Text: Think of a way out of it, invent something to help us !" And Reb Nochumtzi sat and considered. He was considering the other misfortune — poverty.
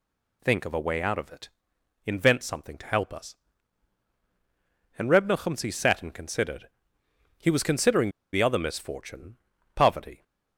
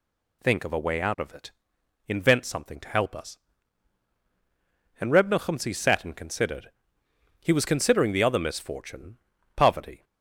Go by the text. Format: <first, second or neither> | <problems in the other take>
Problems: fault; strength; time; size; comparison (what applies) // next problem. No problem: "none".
second | pauses between "considering" and "the"; slight; at 8.0 s; 0.23 s long